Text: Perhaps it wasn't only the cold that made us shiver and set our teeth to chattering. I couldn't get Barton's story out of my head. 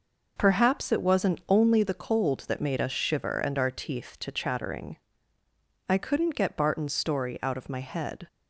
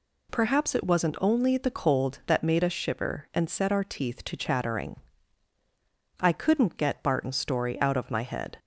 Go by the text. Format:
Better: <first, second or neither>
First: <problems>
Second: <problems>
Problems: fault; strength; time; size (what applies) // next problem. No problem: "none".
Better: second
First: skips "set"; at 3.5 s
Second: none